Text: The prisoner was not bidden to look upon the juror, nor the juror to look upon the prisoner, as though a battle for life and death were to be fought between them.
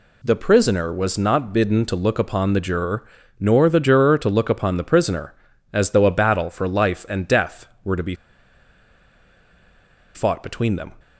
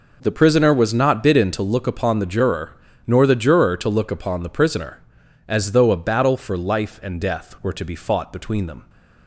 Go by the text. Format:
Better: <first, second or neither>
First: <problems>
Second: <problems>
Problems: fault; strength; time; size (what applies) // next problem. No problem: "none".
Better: second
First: pauses between "be" and "fought"; strong; at 8.1 s; 2.0 s long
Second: none